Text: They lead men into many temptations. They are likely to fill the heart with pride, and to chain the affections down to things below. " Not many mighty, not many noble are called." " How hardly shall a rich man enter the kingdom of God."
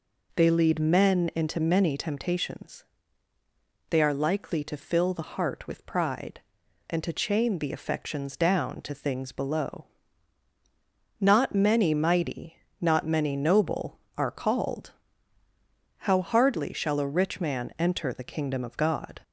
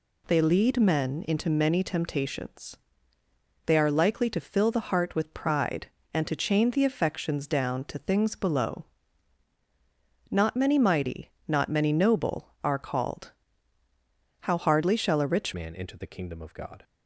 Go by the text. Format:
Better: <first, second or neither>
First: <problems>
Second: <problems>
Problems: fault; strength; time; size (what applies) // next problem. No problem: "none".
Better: first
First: none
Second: changes voice at "man"; from 15.5 s on; 1.3 s long